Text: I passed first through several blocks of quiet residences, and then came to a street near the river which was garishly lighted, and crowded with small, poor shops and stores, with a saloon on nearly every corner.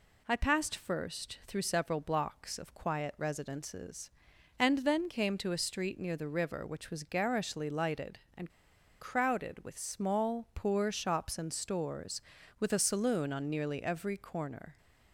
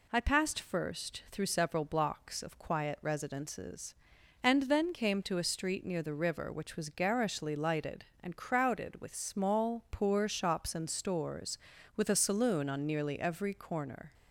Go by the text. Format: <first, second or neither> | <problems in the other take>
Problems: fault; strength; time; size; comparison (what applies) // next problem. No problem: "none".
second | pauses between "and" and "crowded"; noticeable; at 8.4 s; 0.50 s long